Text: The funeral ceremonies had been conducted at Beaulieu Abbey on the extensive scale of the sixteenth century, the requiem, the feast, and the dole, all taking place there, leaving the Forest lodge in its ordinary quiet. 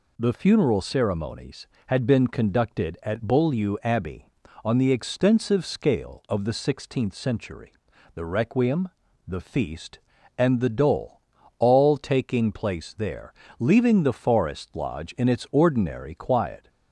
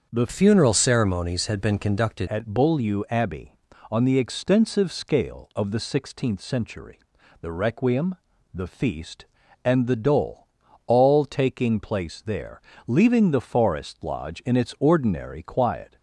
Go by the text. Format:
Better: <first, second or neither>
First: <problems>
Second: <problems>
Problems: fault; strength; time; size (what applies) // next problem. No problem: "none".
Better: first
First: none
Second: starts louder than the rest; until 1.1 s; 6.5 dB // changes voice from "funeral" to "conducted"; from 0.2 to 2.2 s; 2.0 s long